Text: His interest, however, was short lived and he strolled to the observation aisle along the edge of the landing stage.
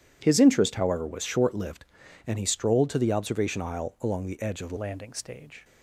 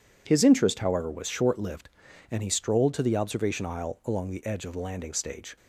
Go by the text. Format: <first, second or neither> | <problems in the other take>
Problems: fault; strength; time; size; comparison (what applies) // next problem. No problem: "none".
second | changes voice at "landing"; from 4.7 s on; 0.9 s long